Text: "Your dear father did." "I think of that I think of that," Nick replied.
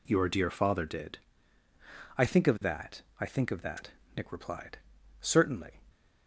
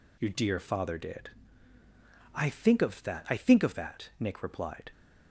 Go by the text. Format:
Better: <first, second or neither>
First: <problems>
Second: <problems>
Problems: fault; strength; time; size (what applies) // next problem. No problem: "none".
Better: second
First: pauses between "that" and "I"; slight; at 3.0 s; 0.18 s long // goes on to say "Certainly"; noticeable; from 5.1 s on; 0.62 s long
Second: none